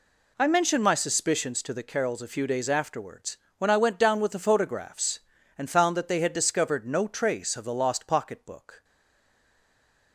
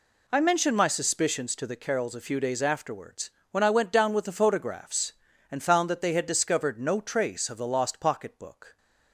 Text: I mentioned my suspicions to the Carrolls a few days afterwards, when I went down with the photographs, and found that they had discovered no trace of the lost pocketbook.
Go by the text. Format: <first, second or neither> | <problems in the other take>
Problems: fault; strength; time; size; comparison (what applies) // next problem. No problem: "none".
second | stays silent after the last word; noticeable; from 8.8 s on; 1.3 s long